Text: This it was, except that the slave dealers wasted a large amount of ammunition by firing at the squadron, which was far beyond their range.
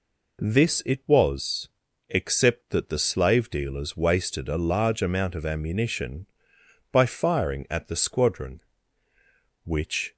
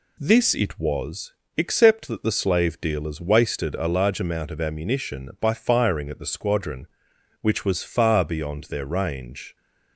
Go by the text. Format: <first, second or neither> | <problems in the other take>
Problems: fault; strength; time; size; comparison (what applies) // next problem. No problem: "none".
second | stops before "was far beyond their range"; at 10.1 s